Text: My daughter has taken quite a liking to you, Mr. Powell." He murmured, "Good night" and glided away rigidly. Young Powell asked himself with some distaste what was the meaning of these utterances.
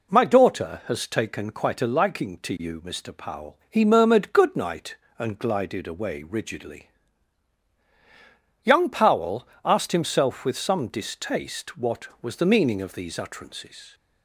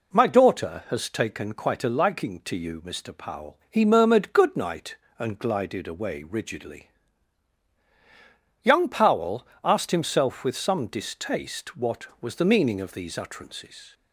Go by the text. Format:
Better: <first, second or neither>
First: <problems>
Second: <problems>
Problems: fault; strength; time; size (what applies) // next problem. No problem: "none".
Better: neither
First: pauses between "Powell" and "asked"; slight; at 9.4 s; 0.18 s long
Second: pauses between "Powell" and "asked"; slight; at 9.4 s; 0.18 s long